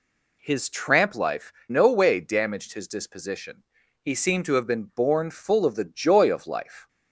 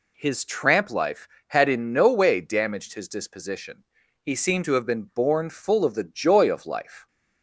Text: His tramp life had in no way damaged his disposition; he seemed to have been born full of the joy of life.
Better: second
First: skips "had in"; at 1.6 s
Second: none

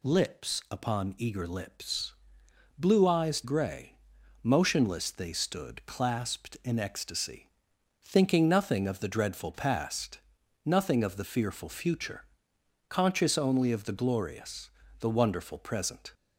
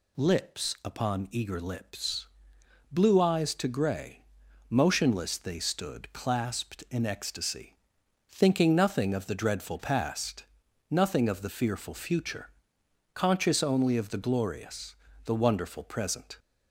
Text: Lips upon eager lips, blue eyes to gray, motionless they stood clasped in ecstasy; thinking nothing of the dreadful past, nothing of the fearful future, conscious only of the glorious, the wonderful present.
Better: second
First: skips "to"; at 3.4 s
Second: none

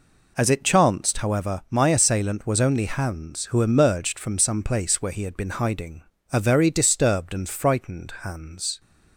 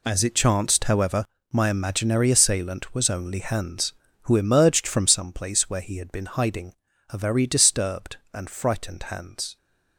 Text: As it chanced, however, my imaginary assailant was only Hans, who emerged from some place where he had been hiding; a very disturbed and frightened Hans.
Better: second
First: skips "imaginary"; at 1.8 s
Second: none

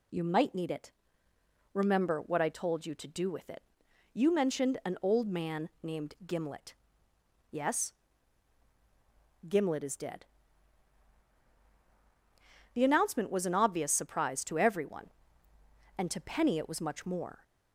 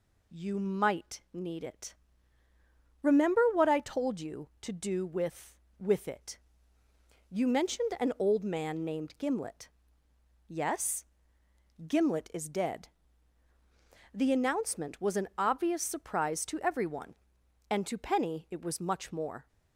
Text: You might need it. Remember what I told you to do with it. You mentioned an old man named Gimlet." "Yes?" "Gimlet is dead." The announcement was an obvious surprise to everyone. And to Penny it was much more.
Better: first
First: none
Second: says "with" twice; at 5.7 s

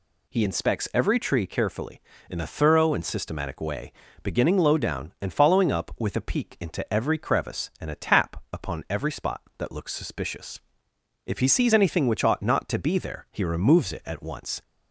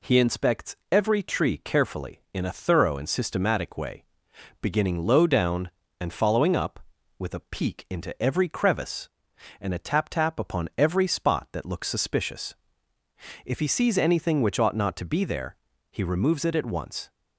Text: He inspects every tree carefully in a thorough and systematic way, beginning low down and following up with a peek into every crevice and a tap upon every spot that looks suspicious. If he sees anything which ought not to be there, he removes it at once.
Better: first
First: none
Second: pauses between "inspects" and "every"; slight; at 0.7 s; 0.16 s long // says "tap" twice; at 10.0 s

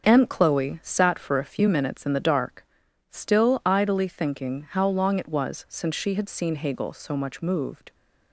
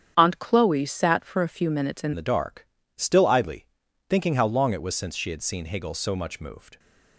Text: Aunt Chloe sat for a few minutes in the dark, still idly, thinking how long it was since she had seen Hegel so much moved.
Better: first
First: starts louder than the rest; until 1.1 s; 7 dB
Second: starts louder than the rest; strong; until 1.2 s; 9 dB // changes voice at "the"; from 2.1 s on; 4.6 s long

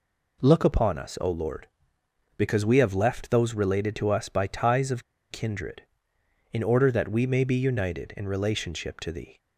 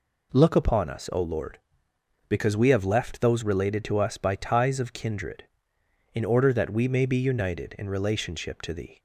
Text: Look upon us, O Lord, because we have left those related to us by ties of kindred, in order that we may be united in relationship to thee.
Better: second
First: pauses between "of" and "kindred"; slight; at 5.0 s; 0.28 s long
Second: none

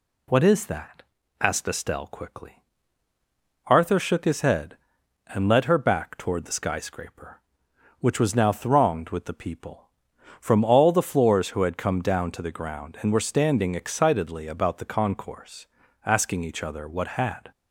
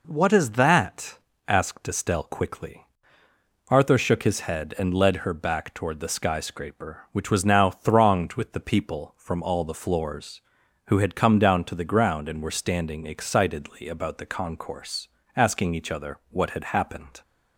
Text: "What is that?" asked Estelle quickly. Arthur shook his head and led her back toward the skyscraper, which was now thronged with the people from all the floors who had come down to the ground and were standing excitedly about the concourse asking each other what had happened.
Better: second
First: pauses between "concourse" and "asking"; at 15.6 s; 0.40 s long // stops before "happened"; at 17.5 s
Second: pauses between "concourse" and "asking"; slight; at 15.0 s; 0.28 s long

